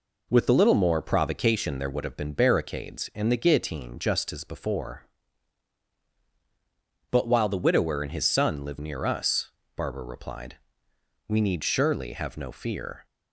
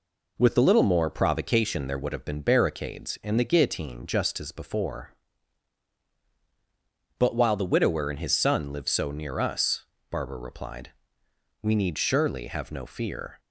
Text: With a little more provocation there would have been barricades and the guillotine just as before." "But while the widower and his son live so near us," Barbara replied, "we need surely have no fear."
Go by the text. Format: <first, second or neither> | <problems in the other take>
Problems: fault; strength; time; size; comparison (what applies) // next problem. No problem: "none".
second | skips "so"; at 8.7 s